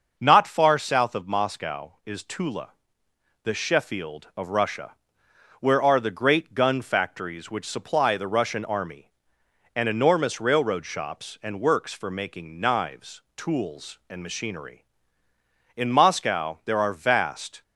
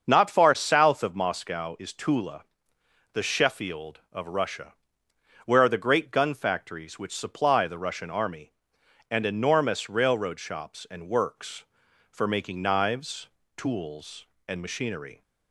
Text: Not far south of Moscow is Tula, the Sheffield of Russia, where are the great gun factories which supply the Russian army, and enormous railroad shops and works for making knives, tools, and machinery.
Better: second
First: starts louder than the rest; until 1.2 s; 6 dB // goes on to say "In Moscow there are vast"; strong; from 15.7 s on; 1.8 s long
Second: starts louder than the rest; until 1.0 s; 6.5 dB

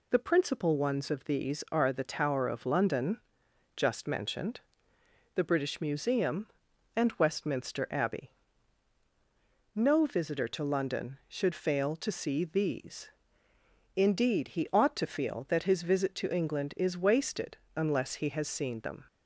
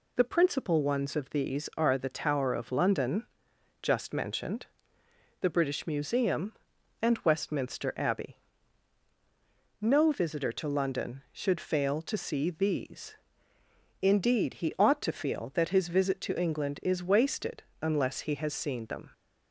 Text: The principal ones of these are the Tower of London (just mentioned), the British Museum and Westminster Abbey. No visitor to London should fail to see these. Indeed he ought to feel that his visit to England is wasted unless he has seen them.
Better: neither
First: pauses between "wasted" and "unless"; slight; at 17.5 s; 0.18 s long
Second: pauses between "wasted" and "unless"; slight; at 17.6 s; 0.18 s long

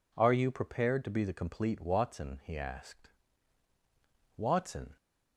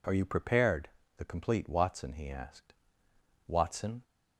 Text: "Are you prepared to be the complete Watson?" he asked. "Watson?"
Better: first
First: none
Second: skips "to be"; at 1.0 s

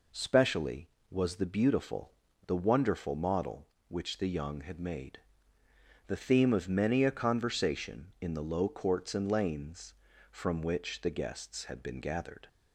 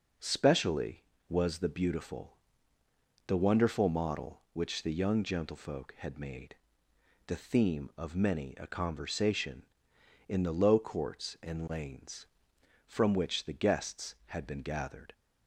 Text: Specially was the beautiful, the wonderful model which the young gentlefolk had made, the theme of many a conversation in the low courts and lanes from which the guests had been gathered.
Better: second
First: skips "gentlefolk"; at 4.6 s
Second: none

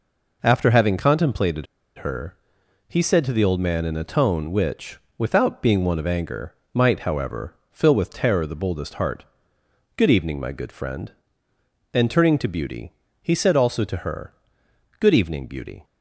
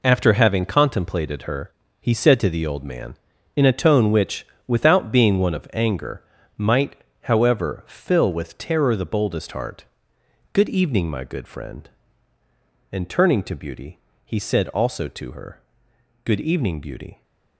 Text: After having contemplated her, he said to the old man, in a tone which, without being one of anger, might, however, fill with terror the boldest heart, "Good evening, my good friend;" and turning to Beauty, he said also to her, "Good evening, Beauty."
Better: second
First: pauses between "contemplated" and "her"; slight; at 1.6 s; 0.32 s long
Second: none

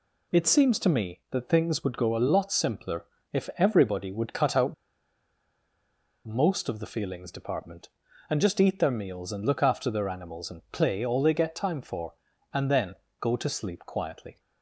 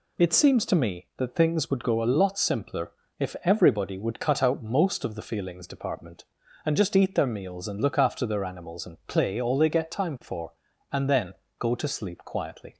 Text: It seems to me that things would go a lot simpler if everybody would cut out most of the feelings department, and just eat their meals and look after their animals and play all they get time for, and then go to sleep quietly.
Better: second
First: pauses between "simpler" and "if"; slight; at 3.0 s; 0.26 s long // pauses between "out" and "most"; strong; at 4.7 s; 1.5 s long // pauses between "then" and "go"; slight; at 12.9 s; 0.26 s long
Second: pauses between "simpler" and "if"; slight; at 2.9 s; 0.26 s long // pauses between "then" and "go"; slight; at 11.3 s; 0.26 s long

